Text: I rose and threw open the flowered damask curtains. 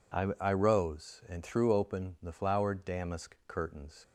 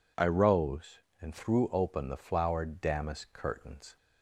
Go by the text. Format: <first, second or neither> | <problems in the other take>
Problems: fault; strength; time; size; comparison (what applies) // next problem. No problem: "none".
second | says "I" twice; at 0.3 s